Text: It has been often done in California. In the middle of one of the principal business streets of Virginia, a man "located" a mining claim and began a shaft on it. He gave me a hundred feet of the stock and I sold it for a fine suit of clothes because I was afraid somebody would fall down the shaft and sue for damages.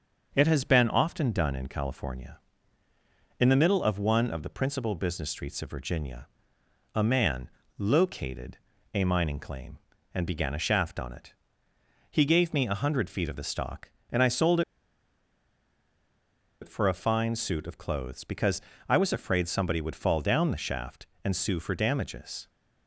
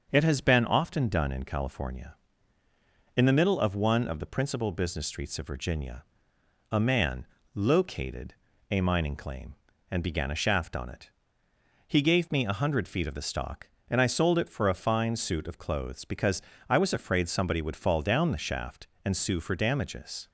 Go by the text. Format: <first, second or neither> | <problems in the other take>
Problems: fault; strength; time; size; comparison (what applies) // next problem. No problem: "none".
second | starts louder than the rest; until 1.3 s; 6.5 dB; also in the second // pauses between "man" and "located"; slight; at 7.4 s; 0.28 s long; slight in the second // pauses between "located" and "a"; slight; at 8.5 s; 0.36 s long; slight in the second // pauses between "sold" and "it"; strong; at 14.6 s; 2.0 s long // pauses between "because" and "I"; slight; at 18.6 s; 0.26 s long; slight in the second